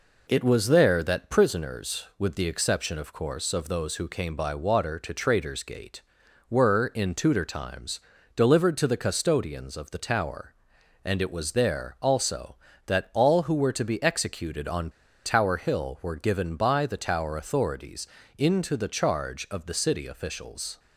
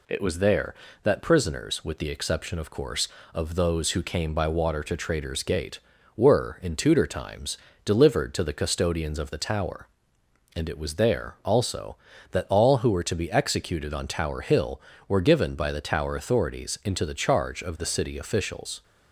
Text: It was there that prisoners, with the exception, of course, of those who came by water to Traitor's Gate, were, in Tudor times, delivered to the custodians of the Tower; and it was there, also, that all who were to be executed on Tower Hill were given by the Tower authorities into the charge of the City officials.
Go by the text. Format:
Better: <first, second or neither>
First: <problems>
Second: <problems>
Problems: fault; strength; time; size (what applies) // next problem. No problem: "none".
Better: second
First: pauses between "on" and "Tower"; at 14.8 s; 0.36 s long // pauses between "authorities" and "into"; slight; at 18.0 s; 0.32 s long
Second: none